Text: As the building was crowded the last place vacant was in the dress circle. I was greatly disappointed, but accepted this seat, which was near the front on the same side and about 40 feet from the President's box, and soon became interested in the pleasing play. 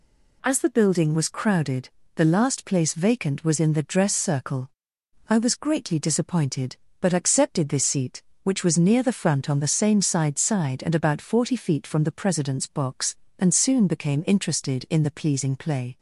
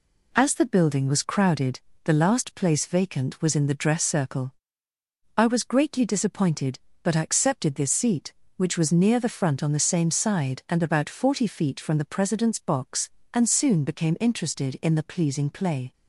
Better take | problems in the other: second | pauses between "crowded" and "the"; slight; at 1.8 s; 0.26 s long; slight in the second // says "side" twice; at 10.3 s

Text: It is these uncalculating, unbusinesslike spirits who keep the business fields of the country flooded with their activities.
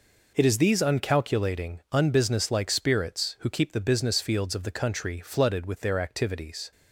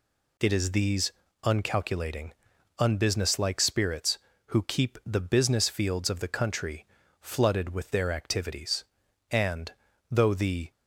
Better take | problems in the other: first | pauses between "these" and "uncalculating"; slight; at 1.1 s; 0.32 s long // pauses between "country" and "flooded"; slight; at 6.8 s; 0.36 s long // goes on to say "And though the"; from 9.3 s on; 1.4 s long

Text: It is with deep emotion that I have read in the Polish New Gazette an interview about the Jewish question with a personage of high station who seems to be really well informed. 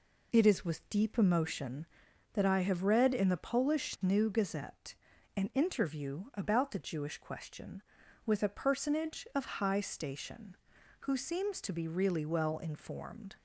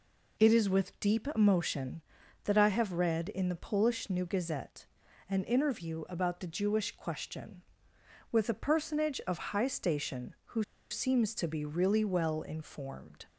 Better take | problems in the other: first | pauses between "Gazette" and "an"; noticeable; at 4.8 s; 0.46 s long; also in the first // pauses between "who" and "seems"; slight; at 10.6 s; 0.27 s long

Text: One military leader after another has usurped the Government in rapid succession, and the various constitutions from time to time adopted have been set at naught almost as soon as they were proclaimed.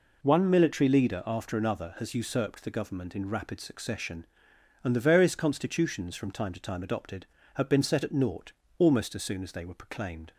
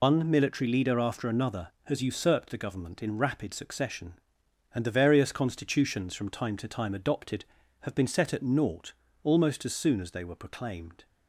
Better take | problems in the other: first | loses the start of "One"; at 0.0 s; 120 ms // pauses between "naught" and "almost"; slight; at 8.9 s; 0.32 s long; slight in the first

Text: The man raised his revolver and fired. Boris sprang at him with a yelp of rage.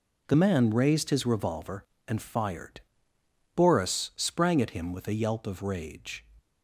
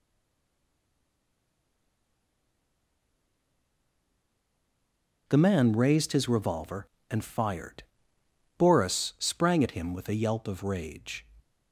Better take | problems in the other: first | stays silent before the first word; strong; until 5.2 s; 5.2 s long

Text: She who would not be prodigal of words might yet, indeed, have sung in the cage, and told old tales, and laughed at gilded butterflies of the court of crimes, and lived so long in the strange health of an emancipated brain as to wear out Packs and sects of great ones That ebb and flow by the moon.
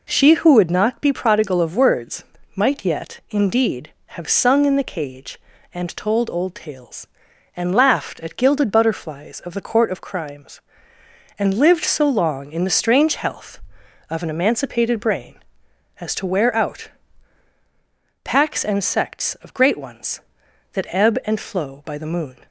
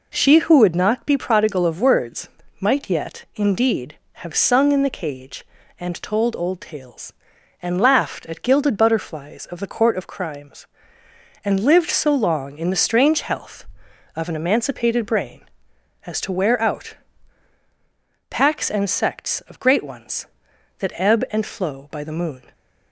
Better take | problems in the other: neither | pauses between "words" and "might"; slight; the same in both // pauses between "out" and "Packs"; strong; the same in both

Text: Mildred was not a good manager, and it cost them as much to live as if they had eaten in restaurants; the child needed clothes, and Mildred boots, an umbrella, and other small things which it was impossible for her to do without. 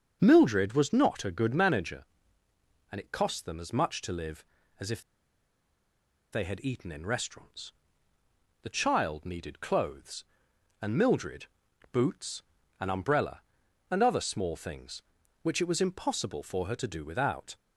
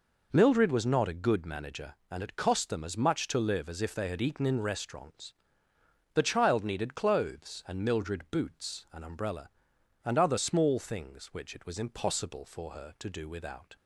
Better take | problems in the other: second | starts louder than the rest; strong; until 1.2 s; 7 dB // pauses between "if" and "they"; strong; at 5.0 s; 1.3 s long // pauses between "Mildred" and "boots"; at 11.4 s; 0.44 s long

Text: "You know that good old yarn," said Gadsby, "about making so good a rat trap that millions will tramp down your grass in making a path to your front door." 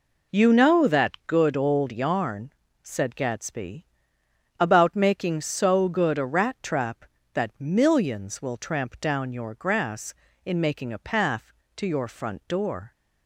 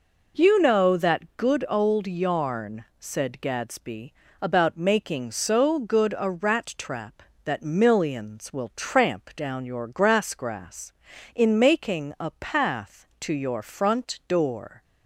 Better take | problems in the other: first | says "grass" twice; at 10.3 s

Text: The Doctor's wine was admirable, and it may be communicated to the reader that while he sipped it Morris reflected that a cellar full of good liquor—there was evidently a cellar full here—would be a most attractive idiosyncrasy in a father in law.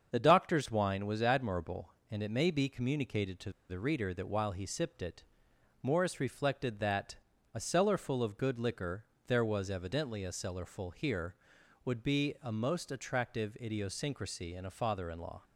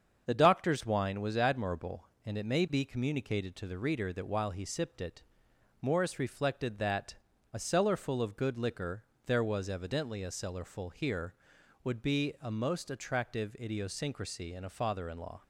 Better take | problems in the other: second | starts louder than the rest; until 1.1 s; 7 dB; also in the second // pauses between "to" and "the"; slight; at 3.5 s; 0.18 s long // pauses between "it" and "Morris"; noticeable; at 5.2 s; 0.58 s long; noticeable in the second // pauses between "that" and "a"; at 7.1 s; 0.38 s long; also in the second

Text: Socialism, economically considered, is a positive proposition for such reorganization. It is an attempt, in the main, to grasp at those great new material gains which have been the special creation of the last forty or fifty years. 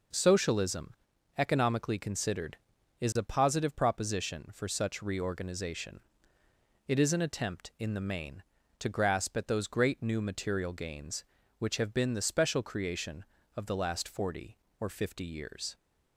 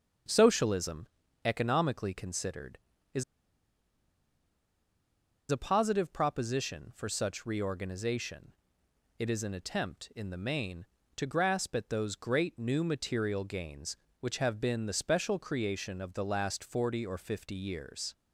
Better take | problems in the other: first | starts louder than the rest; strong; until 1.6 s; 7.5 dB // pauses between "is" and "a"; strong; at 3.2 s; 2.2 s long

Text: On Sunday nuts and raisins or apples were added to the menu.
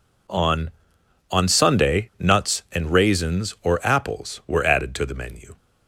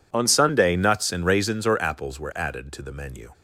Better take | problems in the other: second | says "On" twice; at 1.3 s

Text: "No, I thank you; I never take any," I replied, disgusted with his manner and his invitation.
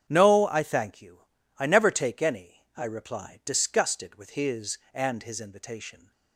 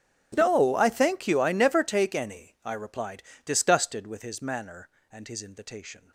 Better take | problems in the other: second | starts louder than the rest; strong; until 1.0 s; 9 dB; strong in the second // skips "manner"; at 4.8 s

